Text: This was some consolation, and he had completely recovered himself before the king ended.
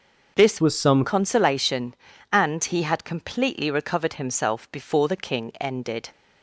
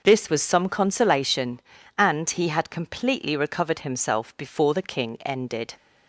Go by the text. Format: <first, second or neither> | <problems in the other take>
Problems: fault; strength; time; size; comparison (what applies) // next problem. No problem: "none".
second | changes voice from "was" to "some"; from 0.6 to 1.0 s; 0.4 s long